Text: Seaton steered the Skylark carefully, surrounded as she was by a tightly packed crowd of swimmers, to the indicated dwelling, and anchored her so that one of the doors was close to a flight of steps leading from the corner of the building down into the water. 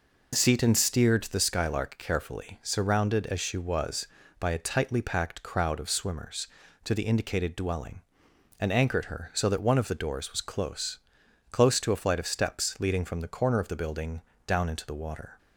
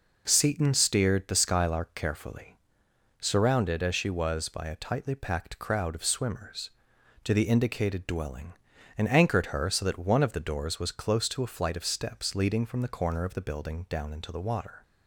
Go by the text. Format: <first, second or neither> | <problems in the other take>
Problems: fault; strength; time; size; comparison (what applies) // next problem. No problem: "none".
second | says "close" twice; at 11.5 s // pauses between "building" and "down"; slight; at 14.2 s; 0.26 s long